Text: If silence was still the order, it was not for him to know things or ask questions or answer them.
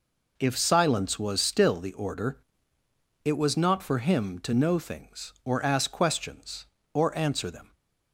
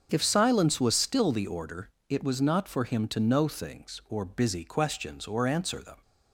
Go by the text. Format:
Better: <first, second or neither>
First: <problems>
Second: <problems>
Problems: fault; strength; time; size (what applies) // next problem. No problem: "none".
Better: first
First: none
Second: starts louder than the rest; strong; until 1.1 s; 7.5 dB // says "busy" for "ask"; at 4.2 s